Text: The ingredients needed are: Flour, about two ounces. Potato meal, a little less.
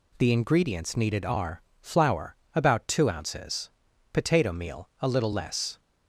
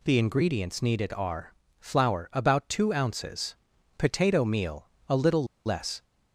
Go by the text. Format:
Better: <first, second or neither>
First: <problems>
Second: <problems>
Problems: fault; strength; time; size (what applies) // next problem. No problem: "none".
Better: first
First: none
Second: pauses between "little" and "less"; slight; at 5.4 s; 0.21 s long